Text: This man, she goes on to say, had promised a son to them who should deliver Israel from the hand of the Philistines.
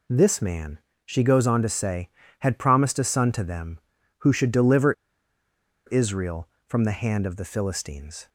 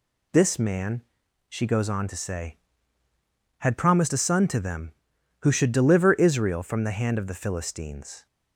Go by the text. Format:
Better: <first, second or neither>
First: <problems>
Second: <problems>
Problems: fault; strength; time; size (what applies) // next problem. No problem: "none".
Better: second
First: pauses between "deliver" and "Israel"; noticeable; at 4.9 s; 0.93 s long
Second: none